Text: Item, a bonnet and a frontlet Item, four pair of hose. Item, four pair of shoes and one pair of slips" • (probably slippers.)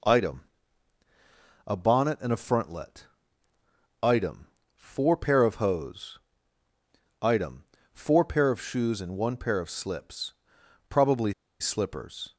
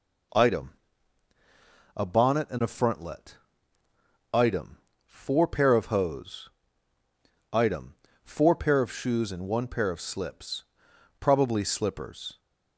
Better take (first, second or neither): second